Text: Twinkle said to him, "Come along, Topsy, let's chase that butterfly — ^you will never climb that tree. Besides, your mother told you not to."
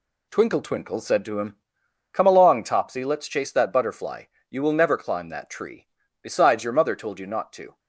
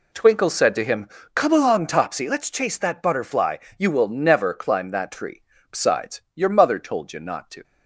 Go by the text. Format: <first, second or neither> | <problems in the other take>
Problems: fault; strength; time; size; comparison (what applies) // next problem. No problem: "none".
second | says "Twinkle" twice; at 0.6 s